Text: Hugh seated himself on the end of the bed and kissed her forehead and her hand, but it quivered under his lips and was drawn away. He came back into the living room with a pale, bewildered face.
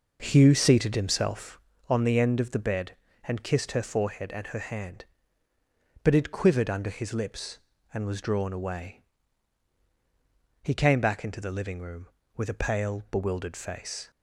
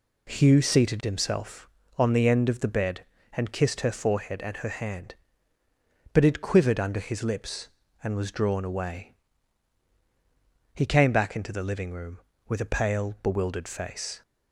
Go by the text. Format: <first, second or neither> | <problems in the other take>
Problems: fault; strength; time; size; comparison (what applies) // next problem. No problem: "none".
second | starts louder than the rest; noticeable; until 1.7 s; 5.5 dB